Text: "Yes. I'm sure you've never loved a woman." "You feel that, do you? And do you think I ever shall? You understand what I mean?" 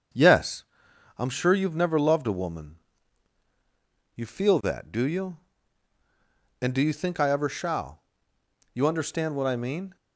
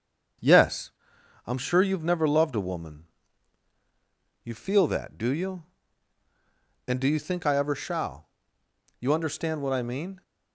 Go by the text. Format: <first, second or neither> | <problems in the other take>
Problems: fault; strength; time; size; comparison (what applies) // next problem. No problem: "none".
neither | starts louder than the rest; the same in both